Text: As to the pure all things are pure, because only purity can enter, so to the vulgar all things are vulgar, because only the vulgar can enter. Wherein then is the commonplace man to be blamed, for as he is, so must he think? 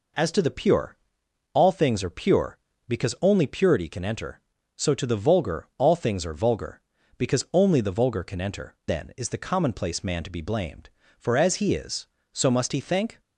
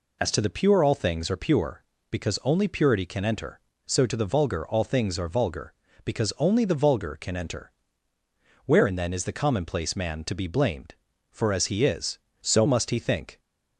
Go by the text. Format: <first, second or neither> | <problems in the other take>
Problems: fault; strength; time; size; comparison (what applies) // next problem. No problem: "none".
second | pauses between "pure" and "all"; noticeable; at 0.9 s; 0.56 s long // skips "Wherein"; at 8.8 s